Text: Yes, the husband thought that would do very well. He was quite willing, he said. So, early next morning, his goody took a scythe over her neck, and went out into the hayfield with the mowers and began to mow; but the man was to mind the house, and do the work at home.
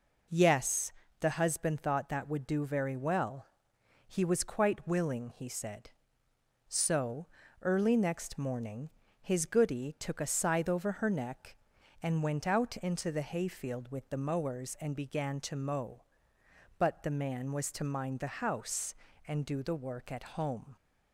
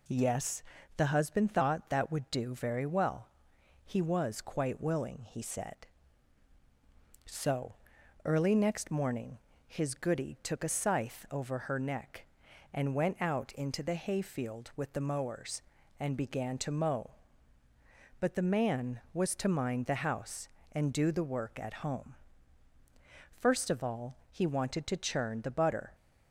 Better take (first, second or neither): first